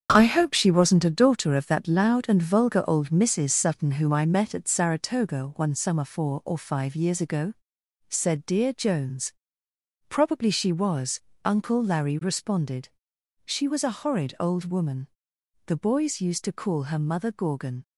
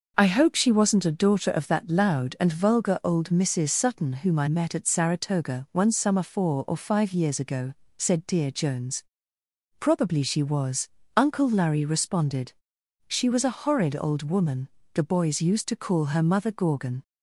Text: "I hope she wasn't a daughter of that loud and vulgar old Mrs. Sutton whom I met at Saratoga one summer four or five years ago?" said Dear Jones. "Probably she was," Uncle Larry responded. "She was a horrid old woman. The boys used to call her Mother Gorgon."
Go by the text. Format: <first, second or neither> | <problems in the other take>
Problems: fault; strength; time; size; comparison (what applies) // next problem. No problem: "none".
second | gets quieter; strong; throughout; 8 dB